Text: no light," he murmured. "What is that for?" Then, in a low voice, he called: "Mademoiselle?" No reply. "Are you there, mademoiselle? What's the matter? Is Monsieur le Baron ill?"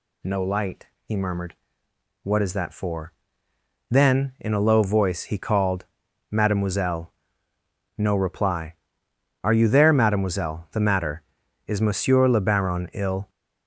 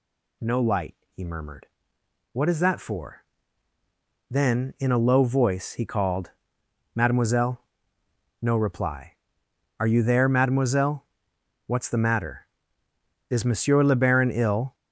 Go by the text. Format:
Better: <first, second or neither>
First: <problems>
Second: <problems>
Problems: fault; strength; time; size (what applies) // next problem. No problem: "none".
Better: second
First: skips "What's"; at 10.7 s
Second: none